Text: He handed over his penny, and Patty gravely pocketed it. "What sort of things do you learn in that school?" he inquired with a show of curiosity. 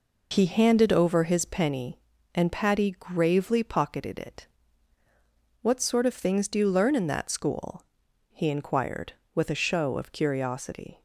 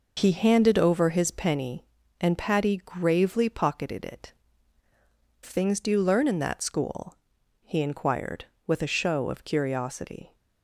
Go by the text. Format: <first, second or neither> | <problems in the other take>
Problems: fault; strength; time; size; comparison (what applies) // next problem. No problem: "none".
first | skips "What sort of"; at 4.8 s